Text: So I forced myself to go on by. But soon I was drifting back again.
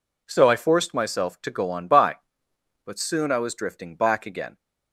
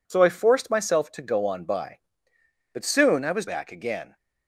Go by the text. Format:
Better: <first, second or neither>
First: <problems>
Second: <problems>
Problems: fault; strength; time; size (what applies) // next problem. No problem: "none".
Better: first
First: none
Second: skips "drifting"; at 3.4 s